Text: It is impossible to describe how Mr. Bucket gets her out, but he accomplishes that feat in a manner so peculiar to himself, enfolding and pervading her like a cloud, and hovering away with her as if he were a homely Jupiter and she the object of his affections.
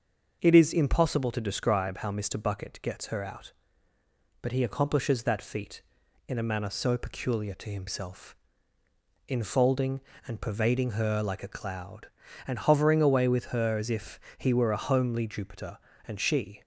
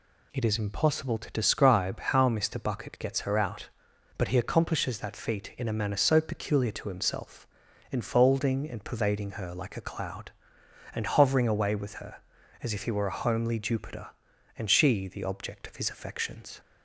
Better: second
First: starts louder than the rest; until 1.4 s; 6.5 dB // pauses between "if" and "he"; slight; at 14.1 s; 0.20 s long // stops before "the object of his affections"; at 16.6 s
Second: none

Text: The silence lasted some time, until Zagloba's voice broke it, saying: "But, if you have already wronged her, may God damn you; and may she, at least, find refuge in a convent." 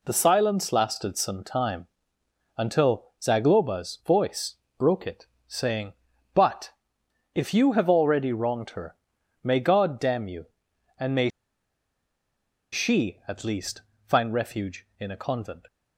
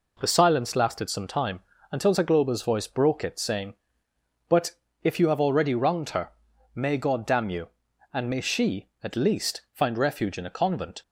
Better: second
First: pauses between "voice" and "broke"; slight; at 4.5 s; 0.24 s long // pauses between "may" and "she"; strong; at 11.2 s; 1.4 s long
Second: none

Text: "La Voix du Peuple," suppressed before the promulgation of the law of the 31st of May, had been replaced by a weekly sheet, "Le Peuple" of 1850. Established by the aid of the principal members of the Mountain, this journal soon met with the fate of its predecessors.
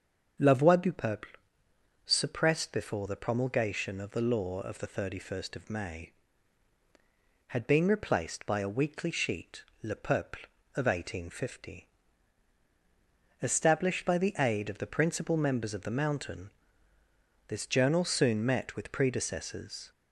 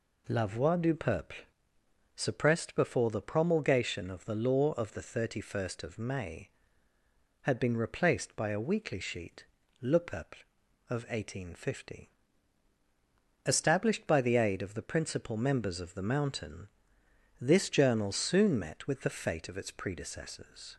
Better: second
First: starts louder than the rest; until 2.1 s; 7 dB // skips "the fate of its"; at 18.9 s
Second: none

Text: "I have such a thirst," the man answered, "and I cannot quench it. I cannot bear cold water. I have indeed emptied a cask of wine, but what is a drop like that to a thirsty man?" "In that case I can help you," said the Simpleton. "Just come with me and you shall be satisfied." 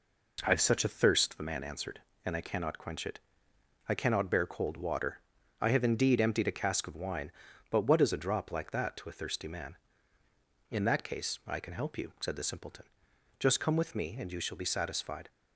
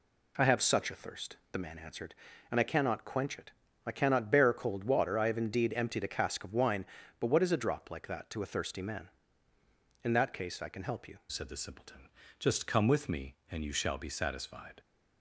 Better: first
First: none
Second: changes voice at "said"; from 11.2 s on; 3.5 s long

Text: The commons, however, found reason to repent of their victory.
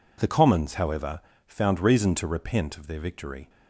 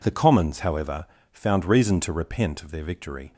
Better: neither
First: none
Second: none

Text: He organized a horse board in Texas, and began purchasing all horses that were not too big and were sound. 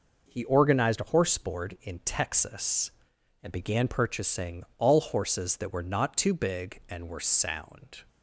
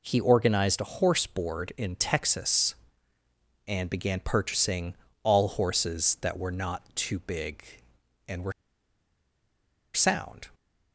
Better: first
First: none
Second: pauses between "purchasing" and "all"; slight; at 4.9 s; 0.28 s long // pauses between "were" and "sound"; strong; at 8.5 s; 1.4 s long

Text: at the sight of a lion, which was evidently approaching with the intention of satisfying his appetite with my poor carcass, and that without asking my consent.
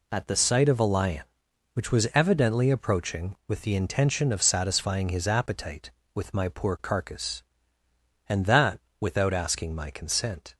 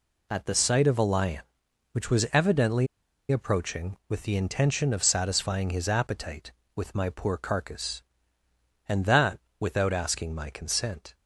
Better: first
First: pauses between "that" and "without"; slight; at 8.7 s; 0.22 s long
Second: pauses between "evidently" and "approaching"; at 2.8 s; 0.45 s long // pauses between "that" and "without"; slight; at 9.3 s; 0.22 s long

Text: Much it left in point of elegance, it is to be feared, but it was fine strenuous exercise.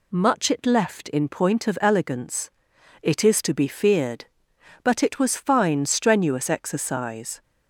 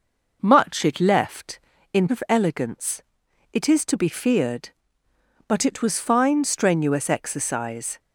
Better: first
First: none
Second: skips "point"; at 2.0 s

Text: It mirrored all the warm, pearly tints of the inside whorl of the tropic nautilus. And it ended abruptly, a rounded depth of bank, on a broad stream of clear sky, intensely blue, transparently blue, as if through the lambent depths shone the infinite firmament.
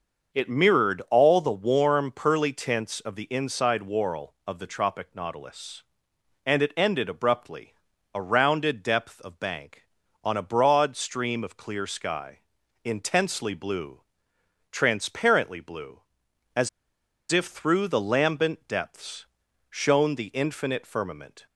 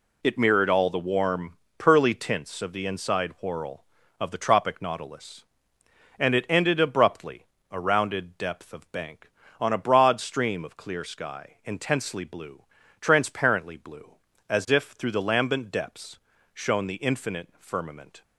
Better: second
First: starts louder than the rest; until 1.4 s; 6.5 dB // pauses between "as" and "if"; noticeable; at 16.6 s; 0.62 s long // pauses between "depths" and "shone"; at 19.2 s; 0.44 s long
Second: pauses between "depths" and "shone"; slight; at 16.1 s; 0.34 s long

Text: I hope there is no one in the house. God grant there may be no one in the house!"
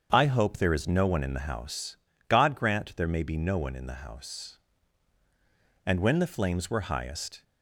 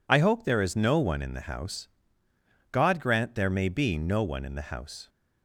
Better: second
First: starts louder than the rest; strong; until 1.1 s; 7 dB // goes on to say "And when the flames were highest"; from 5.8 s on; 1.5 s long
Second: none

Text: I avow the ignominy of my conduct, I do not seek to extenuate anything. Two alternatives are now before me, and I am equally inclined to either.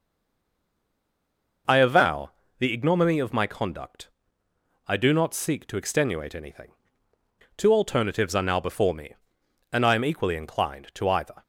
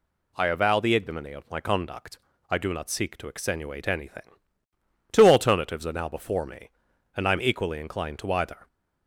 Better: second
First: stays silent before the first word; noticeable; until 1.6 s; 1.6 s long // pauses between "avow" and "the"; slight; at 2.3 s; 0.30 s long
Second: none

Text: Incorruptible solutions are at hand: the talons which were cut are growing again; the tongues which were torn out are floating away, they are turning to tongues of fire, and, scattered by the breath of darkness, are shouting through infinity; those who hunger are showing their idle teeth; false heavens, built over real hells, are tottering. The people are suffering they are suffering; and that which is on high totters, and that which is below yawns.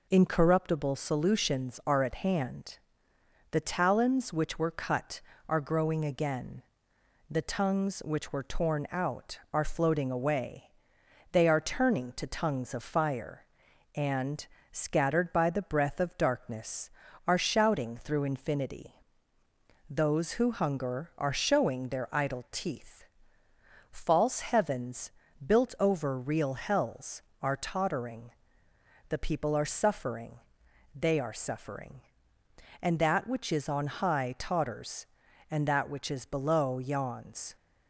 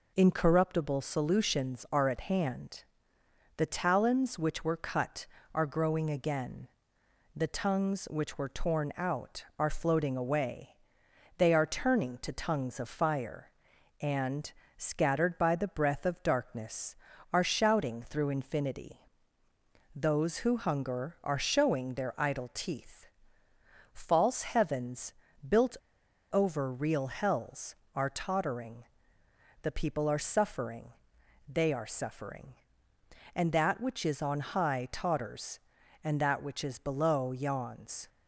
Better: first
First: pauses between "suffering" and "they"; noticeable; at 30.3 s; 0.54 s long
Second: pauses between "built" and "over"; noticeable; at 25.7 s; 0.55 s long // pauses between "suffering" and "they"; noticeable; at 30.9 s; 0.54 s long

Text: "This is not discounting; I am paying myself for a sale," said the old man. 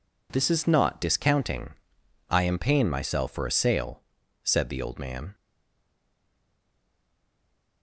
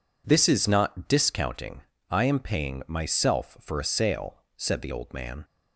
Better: second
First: stays silent after the last word; from 5.3 s on; 2.5 s long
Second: none

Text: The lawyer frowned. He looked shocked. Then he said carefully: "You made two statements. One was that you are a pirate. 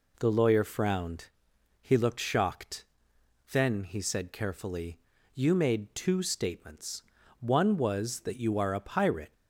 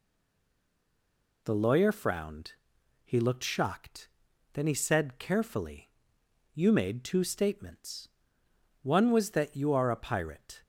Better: first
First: none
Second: stays silent before the first word; noticeable; until 1.4 s; 1.4 s long

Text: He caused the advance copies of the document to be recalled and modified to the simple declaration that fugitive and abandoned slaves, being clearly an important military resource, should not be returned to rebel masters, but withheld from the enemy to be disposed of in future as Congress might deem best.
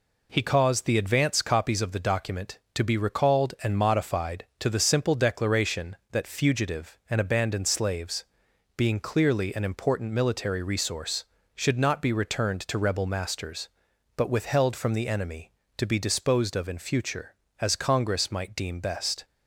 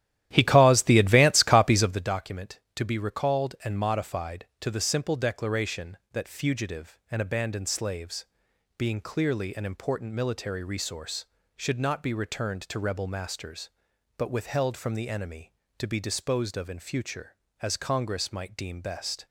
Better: first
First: none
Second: starts louder than the rest; strong; until 2.1 s; 12.5 dB

